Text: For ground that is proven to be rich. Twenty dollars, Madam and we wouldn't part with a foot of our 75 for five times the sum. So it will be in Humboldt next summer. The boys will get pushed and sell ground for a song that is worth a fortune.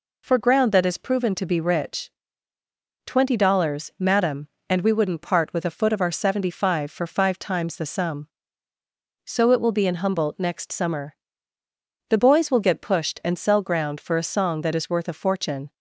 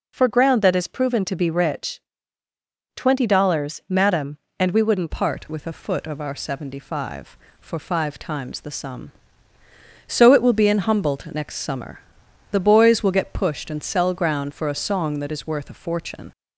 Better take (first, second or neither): first